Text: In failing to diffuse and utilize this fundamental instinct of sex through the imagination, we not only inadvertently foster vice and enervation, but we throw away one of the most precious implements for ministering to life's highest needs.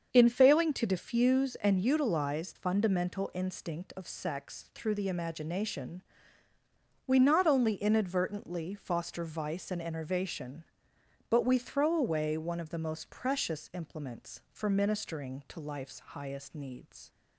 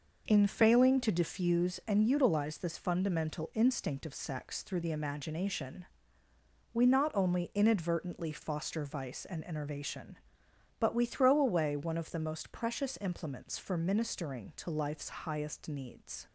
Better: second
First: starts louder than the rest; until 1.1 s; 7 dB // skips "this"; at 2.5 s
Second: none

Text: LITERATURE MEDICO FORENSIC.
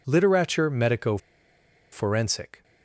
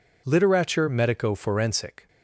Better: second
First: pauses between "MEDICO" and "FORENSIC"; noticeable; at 1.1 s; 0.72 s long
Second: none

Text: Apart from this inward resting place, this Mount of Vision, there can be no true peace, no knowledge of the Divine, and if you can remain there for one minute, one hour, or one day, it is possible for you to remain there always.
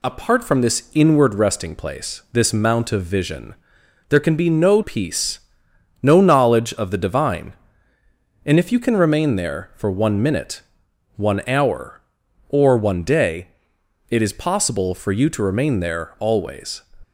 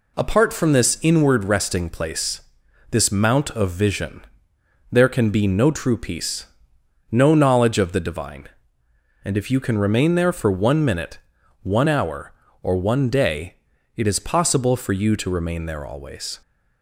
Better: second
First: skips "true"; at 4.8 s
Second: none

